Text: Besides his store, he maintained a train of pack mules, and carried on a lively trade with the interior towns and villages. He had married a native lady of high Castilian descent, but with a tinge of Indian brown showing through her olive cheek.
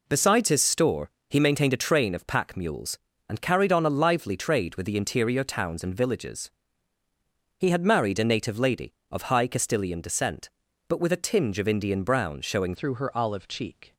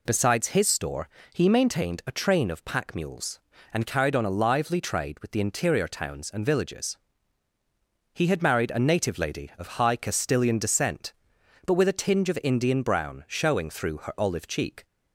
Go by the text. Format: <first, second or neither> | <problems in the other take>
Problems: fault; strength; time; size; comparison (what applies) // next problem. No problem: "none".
second | changes voice at "through"; from 12.7 s on; 1.2 s long